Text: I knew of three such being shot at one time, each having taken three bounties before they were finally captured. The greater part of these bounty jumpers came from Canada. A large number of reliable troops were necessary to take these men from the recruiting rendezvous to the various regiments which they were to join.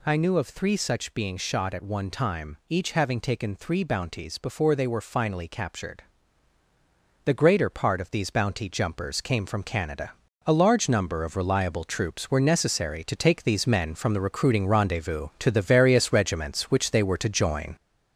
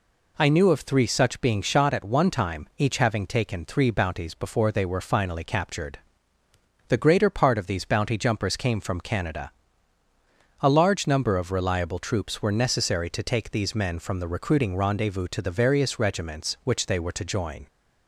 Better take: second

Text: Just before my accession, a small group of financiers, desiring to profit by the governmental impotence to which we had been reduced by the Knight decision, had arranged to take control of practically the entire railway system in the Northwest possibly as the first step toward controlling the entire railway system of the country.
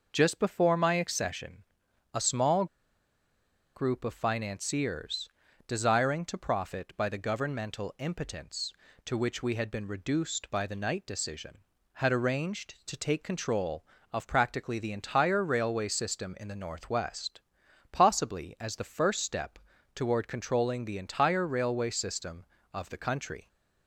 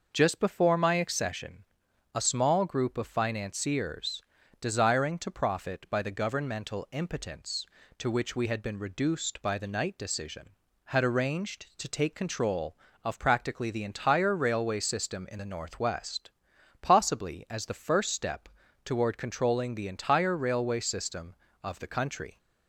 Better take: second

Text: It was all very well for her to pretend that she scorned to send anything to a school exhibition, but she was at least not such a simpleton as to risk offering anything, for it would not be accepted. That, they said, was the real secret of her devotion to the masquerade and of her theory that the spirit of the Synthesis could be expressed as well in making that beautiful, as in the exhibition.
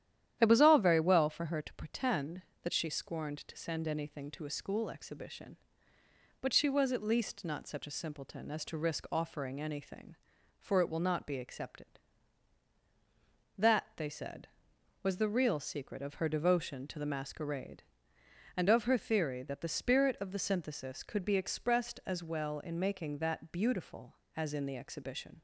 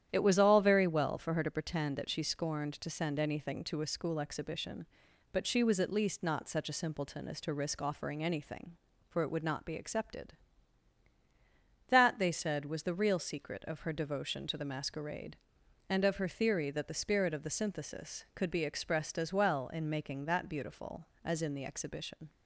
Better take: second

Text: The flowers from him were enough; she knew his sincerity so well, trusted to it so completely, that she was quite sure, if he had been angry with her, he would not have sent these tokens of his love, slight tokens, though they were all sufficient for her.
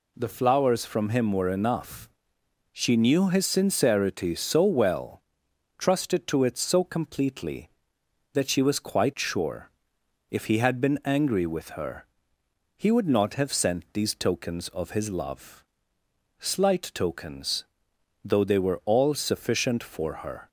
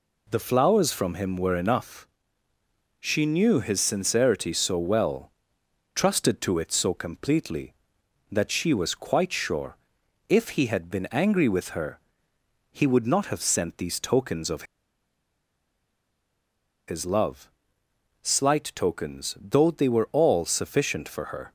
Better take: first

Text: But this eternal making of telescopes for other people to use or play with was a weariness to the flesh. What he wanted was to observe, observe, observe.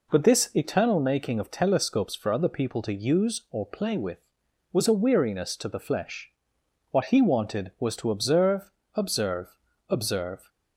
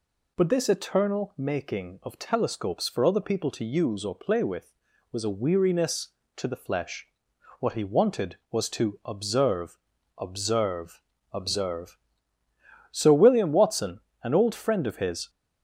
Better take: first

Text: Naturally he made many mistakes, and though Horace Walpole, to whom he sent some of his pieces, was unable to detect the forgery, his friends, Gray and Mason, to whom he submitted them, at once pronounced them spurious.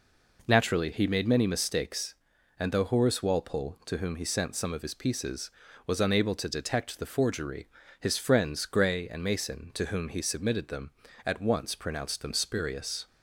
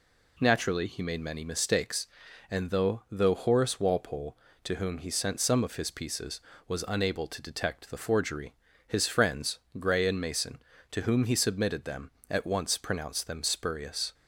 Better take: first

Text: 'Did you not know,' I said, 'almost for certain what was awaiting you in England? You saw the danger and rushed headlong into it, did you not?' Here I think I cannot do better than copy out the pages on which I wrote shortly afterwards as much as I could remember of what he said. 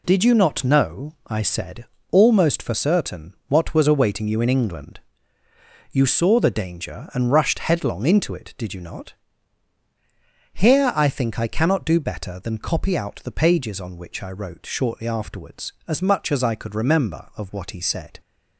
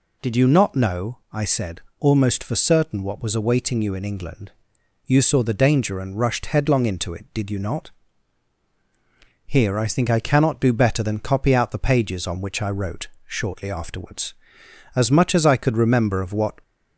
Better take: first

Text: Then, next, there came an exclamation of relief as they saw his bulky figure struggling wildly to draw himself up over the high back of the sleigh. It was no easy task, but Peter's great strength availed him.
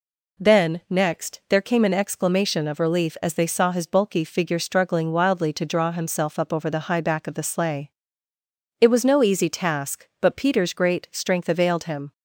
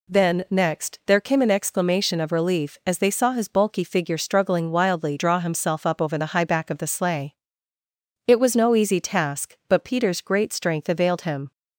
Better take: first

